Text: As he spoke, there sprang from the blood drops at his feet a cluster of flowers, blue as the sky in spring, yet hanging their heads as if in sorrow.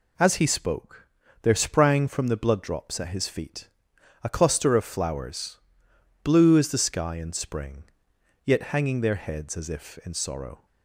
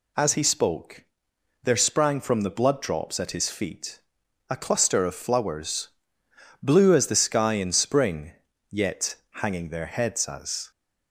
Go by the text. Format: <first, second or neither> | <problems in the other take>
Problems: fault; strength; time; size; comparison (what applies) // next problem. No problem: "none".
first | pauses between "feet" and "a"; noticeable; at 4.0 s; 0.48 s long; noticeable in the first // pauses between "yet" and "hanging"; slight; at 9.1 s; 0.24 s long // stops before "if in sorrow"; at 10.7 s